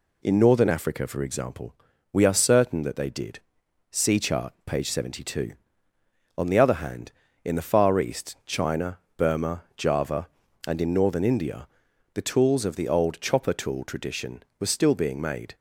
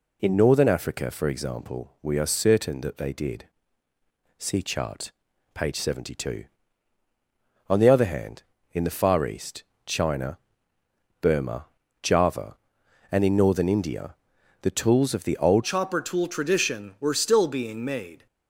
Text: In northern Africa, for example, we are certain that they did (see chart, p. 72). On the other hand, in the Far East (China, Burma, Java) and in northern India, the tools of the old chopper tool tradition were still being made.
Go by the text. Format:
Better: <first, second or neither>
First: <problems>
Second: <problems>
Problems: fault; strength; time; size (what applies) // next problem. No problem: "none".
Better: first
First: none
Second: changes voice at "chopper"; from 15.6 s on; 2.6 s long